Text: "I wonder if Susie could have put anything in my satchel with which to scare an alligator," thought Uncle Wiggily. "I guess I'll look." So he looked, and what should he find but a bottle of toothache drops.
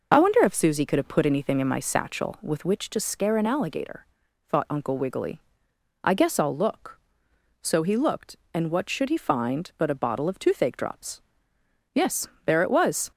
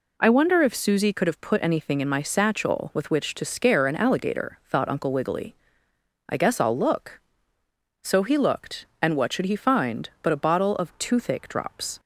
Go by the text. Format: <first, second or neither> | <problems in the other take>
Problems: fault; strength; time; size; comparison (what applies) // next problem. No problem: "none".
second | goes on to say "Yes there it was"; noticeable; from 11.9 s on; 1.1 s long